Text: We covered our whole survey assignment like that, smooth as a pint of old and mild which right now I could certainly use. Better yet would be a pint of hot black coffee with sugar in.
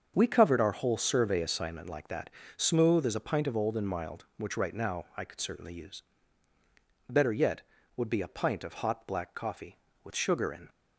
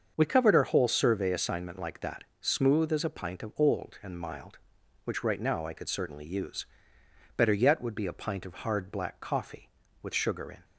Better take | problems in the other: first | starts louder than the rest; until 1.1 s; 6.5 dB; also in the first // says "hard" for "hot"; at 8.5 s

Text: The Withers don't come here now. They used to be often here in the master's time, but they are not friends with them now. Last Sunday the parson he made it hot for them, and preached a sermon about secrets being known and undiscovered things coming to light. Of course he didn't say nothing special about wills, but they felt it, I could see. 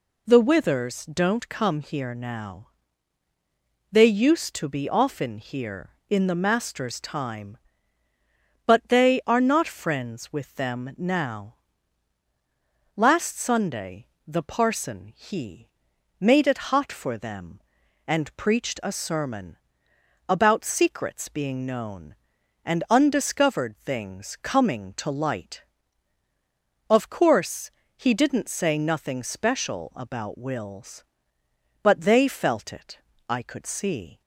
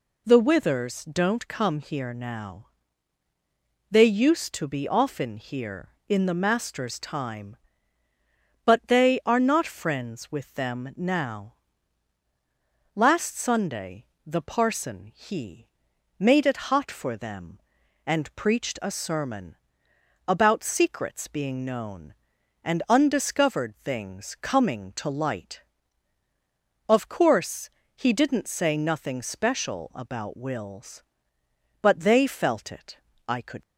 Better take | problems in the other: first | pauses between "Sunday" and "the"; slight; at 14.0 s; 0.22 s long; slight in the first // pauses between "he" and "made"; noticeable; at 15.6 s; 0.52 s long; noticeable in the first // pauses between "sermon" and "about"; noticeable; at 19.5 s; 0.74 s long; noticeable in the first // pauses between "course" and "he"; slight; at 27.7 s; 0.26 s long; slight in the first // stops before "see"; at 33.6 s

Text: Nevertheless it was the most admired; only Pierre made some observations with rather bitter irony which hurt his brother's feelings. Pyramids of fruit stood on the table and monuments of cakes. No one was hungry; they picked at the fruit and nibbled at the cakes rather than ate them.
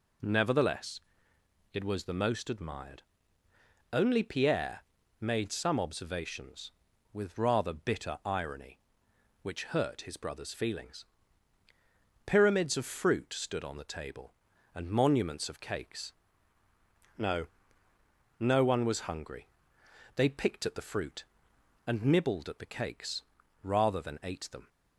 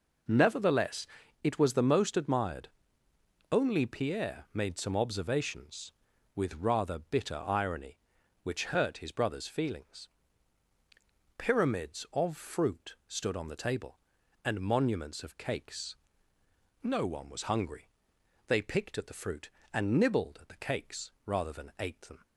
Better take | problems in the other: second | pauses between "Nevertheless" and "it"; noticeable; at 1.0 s; 0.72 s long; also in the second // pauses between "Pierre" and "made"; slight; at 4.8 s; 0.34 s long // says "No" twice; at 18.3 s // pauses between "cakes" and "rather"; at 23.2 s; 0.40 s long

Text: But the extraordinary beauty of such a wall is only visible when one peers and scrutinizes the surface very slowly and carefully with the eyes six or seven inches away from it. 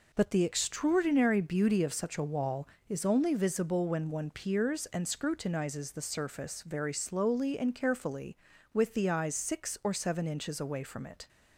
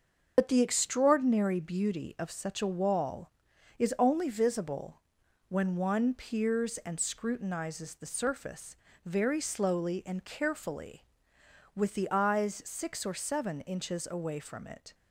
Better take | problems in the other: first | loses the start of "But"; at 0.3 s; 80 ms // starts louder than the rest; until 1.3 s; 6.5 dB // pauses between "visible" and "when"; noticeable; at 5.0 s; 0.48 s long // pauses between "surface" and "very"; slight; at 8.7 s; 0.30 s long

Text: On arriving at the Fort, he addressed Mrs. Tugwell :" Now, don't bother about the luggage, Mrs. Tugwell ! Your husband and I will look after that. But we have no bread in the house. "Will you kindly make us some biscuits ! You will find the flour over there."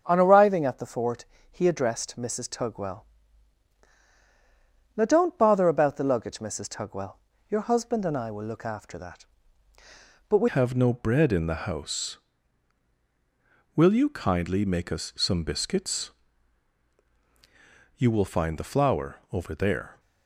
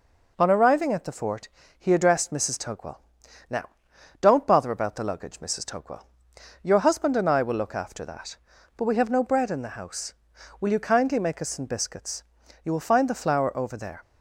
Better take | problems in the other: second | starts louder than the rest; until 1.0 s; 7 dB // changes voice at "have"; from 10.4 s on; 9.5 s long

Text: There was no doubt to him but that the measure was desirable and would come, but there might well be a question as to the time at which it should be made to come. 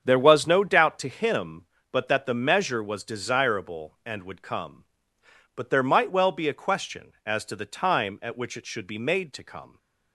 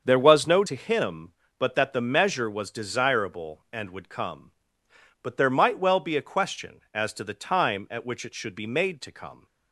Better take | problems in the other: first | starts louder than the rest; until 1.0 s; 7 dB; strong in the first // skips "doubt"; at 0.6 s

